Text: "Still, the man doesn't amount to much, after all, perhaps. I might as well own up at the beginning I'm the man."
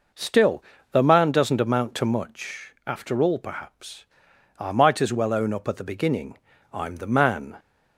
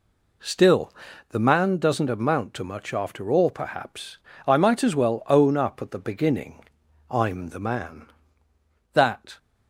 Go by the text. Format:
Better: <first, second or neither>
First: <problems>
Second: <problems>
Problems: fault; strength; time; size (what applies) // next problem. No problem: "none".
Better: first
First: pauses between "beginning" and "I'm"; at 6.3 s; 0.38 s long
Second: pauses between "beginning" and "I'm"; at 6.6 s; 0.44 s long // goes on to say "That"; slight; from 8.9 s on; 0.44 s long